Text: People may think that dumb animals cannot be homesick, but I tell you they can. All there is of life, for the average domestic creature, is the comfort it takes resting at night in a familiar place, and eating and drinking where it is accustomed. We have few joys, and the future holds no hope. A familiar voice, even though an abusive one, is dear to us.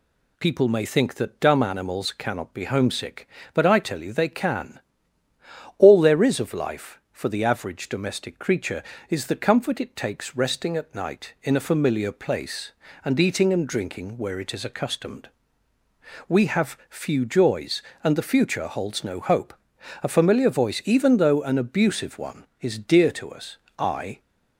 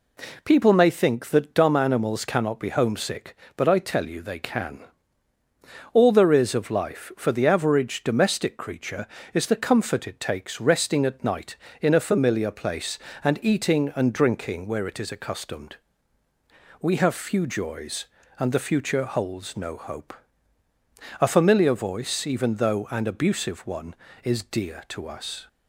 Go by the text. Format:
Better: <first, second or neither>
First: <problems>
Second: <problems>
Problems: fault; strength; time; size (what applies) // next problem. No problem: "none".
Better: second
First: goes on to say "I"; slight; from 23.7 s on; 0.40 s long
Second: none